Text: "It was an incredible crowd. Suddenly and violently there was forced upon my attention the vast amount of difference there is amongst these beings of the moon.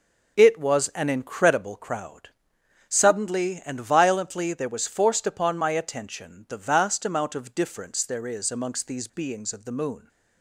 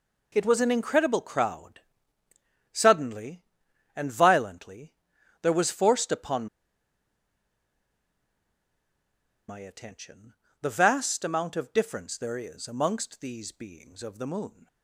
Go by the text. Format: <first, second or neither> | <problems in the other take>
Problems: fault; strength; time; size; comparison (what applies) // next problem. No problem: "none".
first | pauses between "violently" and "there"; noticeable; at 4.9 s; 0.50 s long // pauses between "upon" and "my"; strong; at 6.4 s; 3.0 s long // pauses between "attention" and "the"; slight; at 10.3 s; 0.26 s long